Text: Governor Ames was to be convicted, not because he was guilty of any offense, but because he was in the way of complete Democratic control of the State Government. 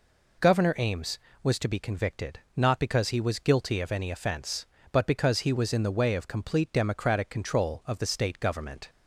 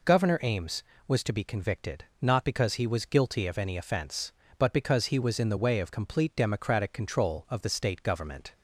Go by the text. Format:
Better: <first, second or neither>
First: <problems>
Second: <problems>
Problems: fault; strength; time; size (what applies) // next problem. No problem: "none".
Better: neither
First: none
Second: none